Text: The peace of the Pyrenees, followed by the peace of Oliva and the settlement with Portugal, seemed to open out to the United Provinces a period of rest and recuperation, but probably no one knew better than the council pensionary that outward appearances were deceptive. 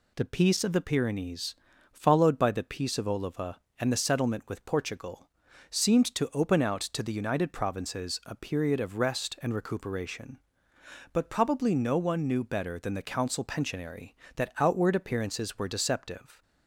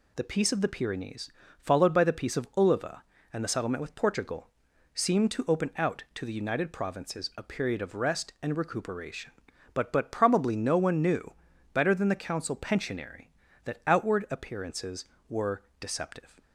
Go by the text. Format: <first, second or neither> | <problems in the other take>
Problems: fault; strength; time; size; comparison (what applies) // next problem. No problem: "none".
first | says "but" twice; at 9.9 s // pauses between "knew" and "better"; at 11.3 s; 0.40 s long // pauses between "were" and "deceptive"; slight; at 15.6 s; 0.16 s long